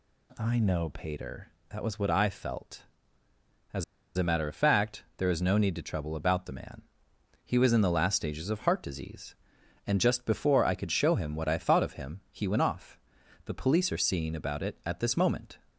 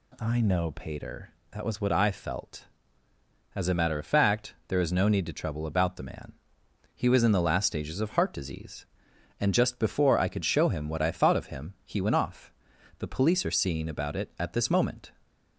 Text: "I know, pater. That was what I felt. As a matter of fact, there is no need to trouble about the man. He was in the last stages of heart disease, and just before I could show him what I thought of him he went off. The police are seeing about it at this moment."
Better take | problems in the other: second | pauses between "As" and "a"; slight; at 3.8 s; 0.31 s long

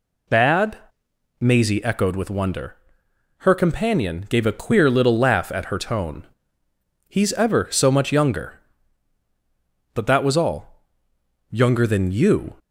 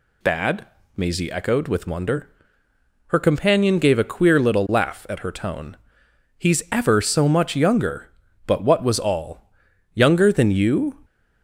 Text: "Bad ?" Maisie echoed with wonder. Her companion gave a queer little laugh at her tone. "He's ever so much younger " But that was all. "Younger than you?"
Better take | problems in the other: first | says "what" for "that"; at 8.6 s

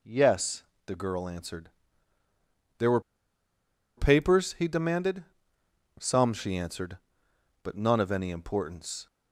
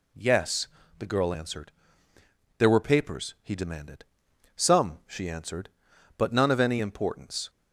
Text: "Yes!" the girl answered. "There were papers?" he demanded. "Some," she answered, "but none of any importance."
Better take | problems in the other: second | pauses between "were" and "papers"; noticeable; at 2.9 s; 0.97 s long

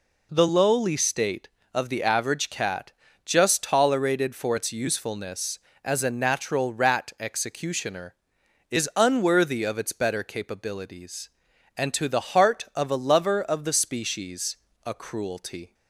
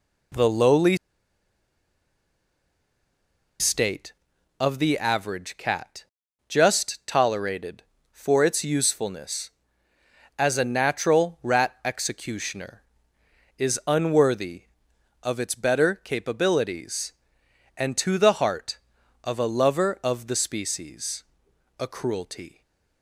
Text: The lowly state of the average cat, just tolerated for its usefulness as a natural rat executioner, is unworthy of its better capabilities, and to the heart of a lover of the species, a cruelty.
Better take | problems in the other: first | pauses between "lowly" and "state"; strong; at 0.9 s; 2.6 s long

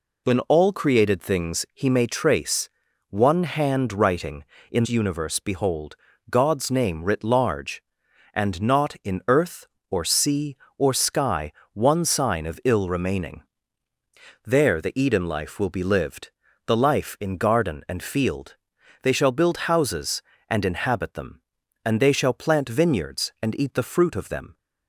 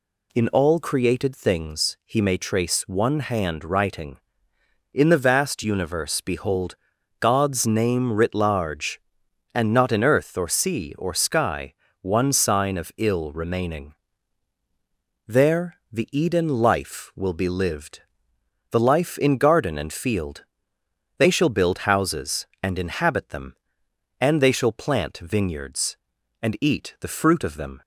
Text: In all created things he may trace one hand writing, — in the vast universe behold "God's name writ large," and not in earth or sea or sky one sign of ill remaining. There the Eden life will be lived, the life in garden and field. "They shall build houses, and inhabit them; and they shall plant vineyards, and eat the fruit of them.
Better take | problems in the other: second | pauses between "trace" and "one"; at 2.6 s; 0.40 s long // skips "the vast"; at 4.8 s // pauses between "behold" and "God's"; slight; at 5.9 s; 0.34 s long; also in the second // pauses between "sky" and "one"; slight; at 11.5 s; 0.18 s long; slight in the second

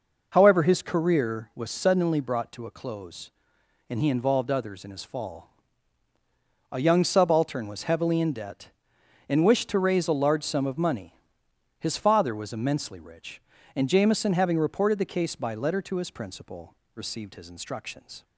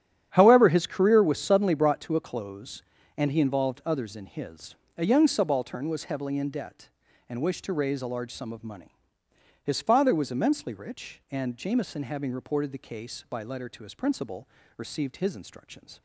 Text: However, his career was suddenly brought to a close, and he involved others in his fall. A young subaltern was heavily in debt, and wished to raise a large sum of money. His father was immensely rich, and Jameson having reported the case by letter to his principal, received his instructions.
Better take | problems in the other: first | starts louder than the rest; strong; until 1.3 s; 10 dB // skips "fall"; at 4.8 s

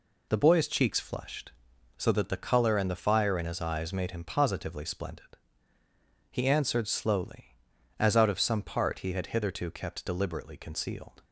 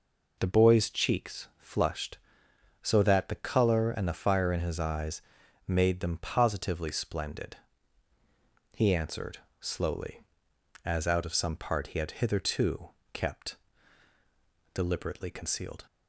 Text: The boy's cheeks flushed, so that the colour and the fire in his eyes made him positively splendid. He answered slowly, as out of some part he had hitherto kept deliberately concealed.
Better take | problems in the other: first | pauses between "eyes" and "made"; noticeable; at 5.2 s; 0.46 s long // says "them" for "him"; at 5.9 s // pauses between "answered" and "slowly"; slight; at 9.3 s; 0.20 s long // pauses between "hitherto" and "kept"; slight; at 12.8 s; 0.24 s long // pauses between "kept" and "deliberately"; at 13.5 s; 1.1 s long

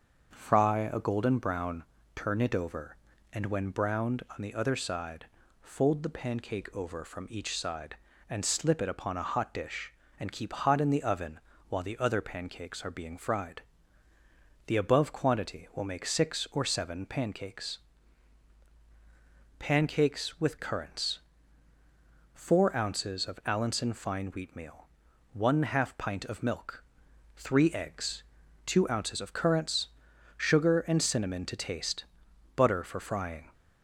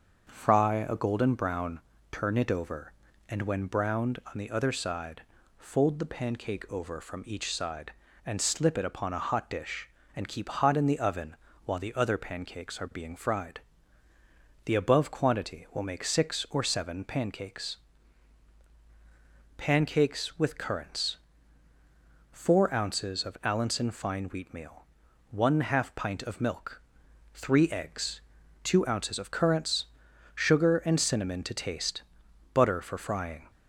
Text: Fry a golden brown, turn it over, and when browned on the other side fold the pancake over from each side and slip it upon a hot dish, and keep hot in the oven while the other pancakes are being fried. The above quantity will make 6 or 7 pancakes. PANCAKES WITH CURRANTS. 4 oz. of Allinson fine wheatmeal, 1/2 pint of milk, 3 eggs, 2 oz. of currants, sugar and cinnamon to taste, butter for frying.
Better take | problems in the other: neither | starts louder than the rest; the same in both // pauses between "side" and "fold"; slight; the same in both // pauses between "oven" and "while"; slight; the same in both

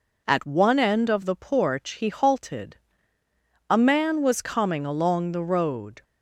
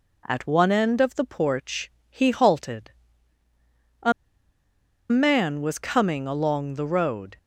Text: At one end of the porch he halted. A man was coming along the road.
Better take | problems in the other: first | pauses between "porch" and "he"; slight; at 1.9 s; 0.18 s long // pauses between "A" and "man"; at 4.1 s; 0.98 s long

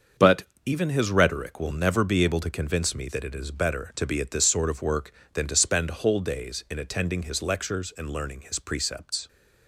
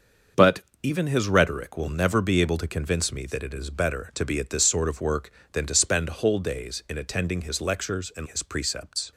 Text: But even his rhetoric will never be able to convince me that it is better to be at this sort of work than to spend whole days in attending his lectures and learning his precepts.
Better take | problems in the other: first | starts louder than the rest; until 1.5 s; 6.5 dB; also in the first // pauses between "But" and "even"; slight; at 0.6 s; 0.22 s long; slight in the first // skips "learning"; at 8.2 s

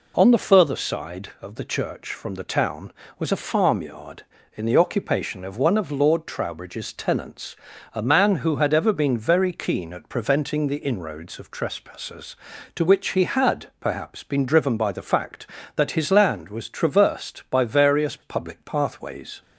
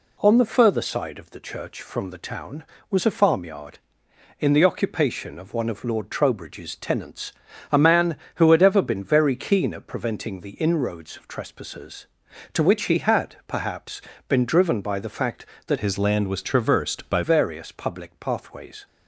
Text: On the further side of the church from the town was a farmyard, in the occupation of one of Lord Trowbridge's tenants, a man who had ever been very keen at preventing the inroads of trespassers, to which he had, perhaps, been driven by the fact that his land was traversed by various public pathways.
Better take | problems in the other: first | changes voice from "his" to "by"; from 15.7 to 17.2 s; 1.5 s long

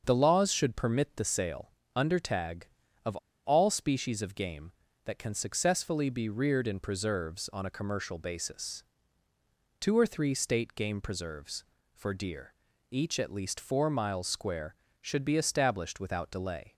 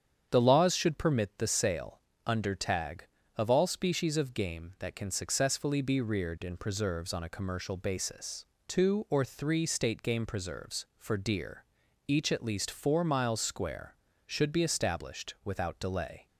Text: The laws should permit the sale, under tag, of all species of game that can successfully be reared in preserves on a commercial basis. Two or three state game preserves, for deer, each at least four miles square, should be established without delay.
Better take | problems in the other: second | starts louder than the rest; until 1.0 s; 7 dB; strong in the second // pauses between "of" and "all"; slight; at 3.1 s; 0.28 s long

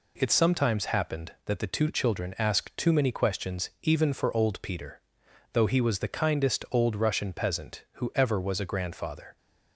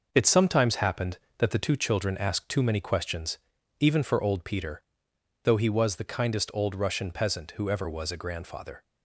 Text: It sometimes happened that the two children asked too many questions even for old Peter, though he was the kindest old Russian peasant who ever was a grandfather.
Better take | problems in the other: first | gets quieter; noticeable; throughout; 6 dB // pauses between "questions" and "even"; at 3.3 s; 0.44 s long

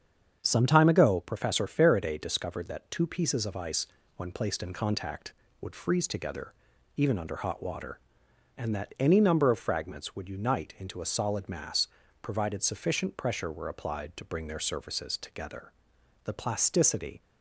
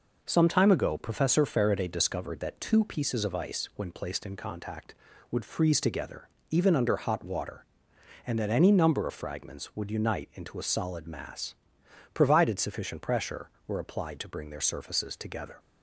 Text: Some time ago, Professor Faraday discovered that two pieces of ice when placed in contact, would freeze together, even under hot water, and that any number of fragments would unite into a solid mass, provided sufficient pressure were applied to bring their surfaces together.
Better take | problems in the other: second | starts louder than the rest; strong; until 1.4 s; 7.5 dB // pauses between "ice" and "when"; slight; at 3.8 s; 0.30 s long // goes on to say "The plasticity"; noticeable; from 16.2 s on; 0.96 s long

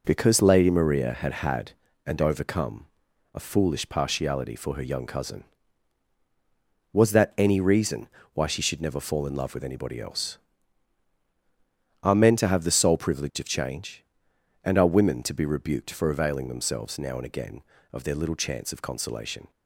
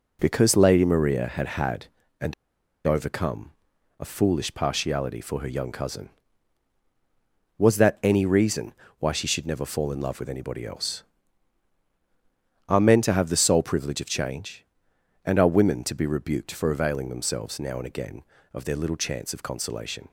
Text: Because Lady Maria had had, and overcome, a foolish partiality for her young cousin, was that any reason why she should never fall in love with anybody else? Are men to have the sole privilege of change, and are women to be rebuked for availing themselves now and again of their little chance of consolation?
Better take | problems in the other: first | pauses between "and" and "overcome"; noticeable; at 2.3 s; 0.53 s long // pauses between "reason" and "why"; slight; at 8.7 s; 0.26 s long; slight in the first

